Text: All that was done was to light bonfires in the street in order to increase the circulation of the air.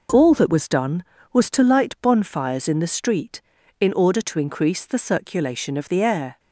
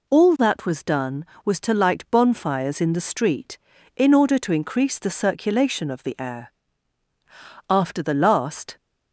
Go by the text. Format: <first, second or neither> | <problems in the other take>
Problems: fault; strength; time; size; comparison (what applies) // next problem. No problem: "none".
first | goes on to say "After the last"; noticeable; from 7.6 s on; 1.0 s long